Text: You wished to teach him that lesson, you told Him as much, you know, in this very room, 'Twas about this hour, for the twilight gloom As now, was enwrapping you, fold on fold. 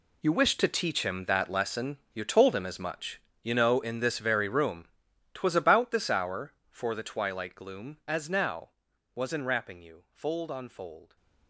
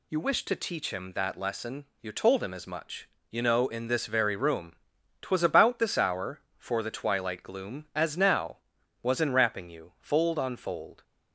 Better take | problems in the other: second | gets quieter; strong; throughout; 13.5 dB

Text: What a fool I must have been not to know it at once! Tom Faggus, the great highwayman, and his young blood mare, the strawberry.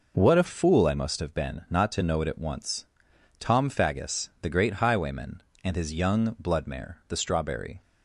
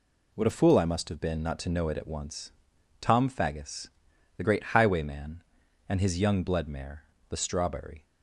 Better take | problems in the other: neither | none

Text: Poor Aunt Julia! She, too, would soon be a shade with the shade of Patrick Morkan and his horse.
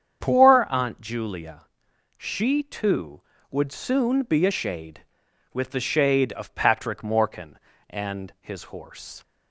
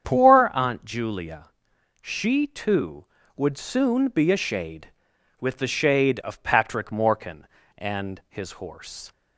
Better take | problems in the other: neither | starts louder than the rest; strong; the same in both

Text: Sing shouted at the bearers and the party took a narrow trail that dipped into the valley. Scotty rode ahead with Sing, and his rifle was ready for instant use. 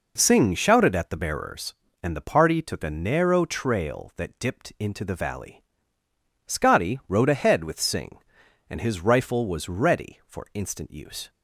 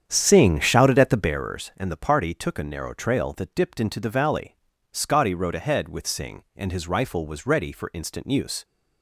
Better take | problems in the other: first | starts louder than the rest; strong; until 1.4 s; 8.5 dB

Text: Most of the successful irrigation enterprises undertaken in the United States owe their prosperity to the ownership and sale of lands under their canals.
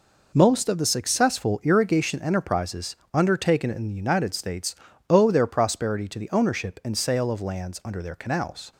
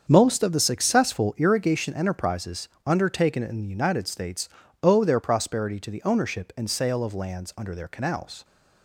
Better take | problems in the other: first | starts louder than the rest; strong; until 1.3 s; 7 dB // pauses between "enterprises" and "undertaken"; slight; at 2.6 s; 0.18 s long; slight in the first // pauses between "States" and "owe"; slight; at 4.4 s; 0.32 s long; slight in the first

